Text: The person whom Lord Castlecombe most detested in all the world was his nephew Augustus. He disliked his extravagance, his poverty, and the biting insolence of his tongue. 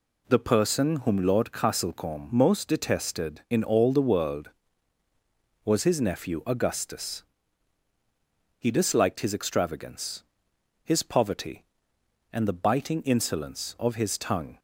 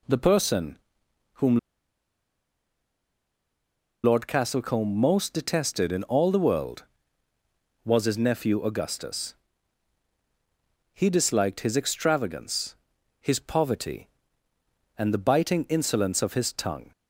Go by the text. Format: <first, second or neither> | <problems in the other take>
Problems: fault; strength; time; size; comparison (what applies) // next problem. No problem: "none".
first | pauses between "person" and "whom"; noticeable; at 0.7 s; 0.56 s long // pauses between "whom" and "Lord"; strong; at 1.5 s; 2.4 s long